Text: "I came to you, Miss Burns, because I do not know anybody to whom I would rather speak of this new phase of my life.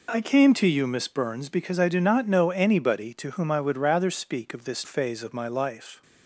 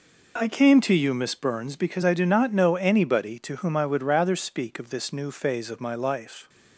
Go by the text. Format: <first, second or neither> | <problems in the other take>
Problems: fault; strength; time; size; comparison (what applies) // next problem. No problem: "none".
second | skips "new"; at 4.8 s